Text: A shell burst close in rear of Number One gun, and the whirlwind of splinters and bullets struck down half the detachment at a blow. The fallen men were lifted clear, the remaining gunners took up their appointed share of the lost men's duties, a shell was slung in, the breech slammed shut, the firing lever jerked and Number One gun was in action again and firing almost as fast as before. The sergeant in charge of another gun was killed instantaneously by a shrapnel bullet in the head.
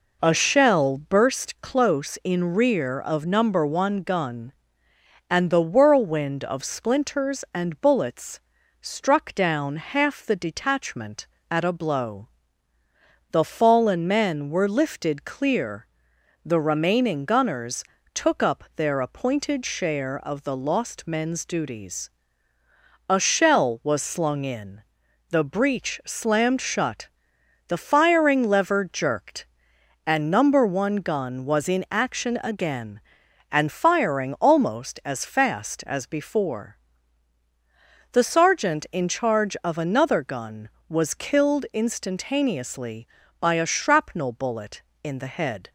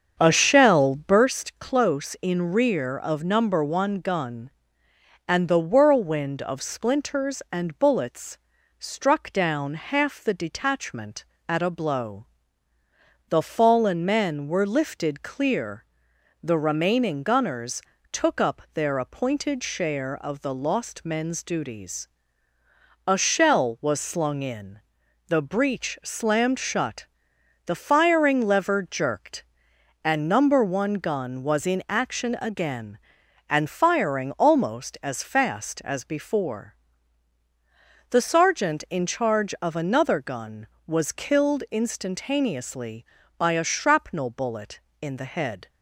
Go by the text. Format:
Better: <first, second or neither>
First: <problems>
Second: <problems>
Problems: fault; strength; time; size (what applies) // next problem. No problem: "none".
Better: first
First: pauses between "bullets" and "struck"; at 8.3 s; 0.42 s long // pauses between "gunners" and "took"; slight; at 17.8 s; 0.32 s long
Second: starts louder than the rest; until 1.4 s; 7 dB // pauses between "bullets" and "struck"; at 8.3 s; 0.42 s long // pauses between "gunners" and "took"; slight; at 17.8 s; 0.32 s long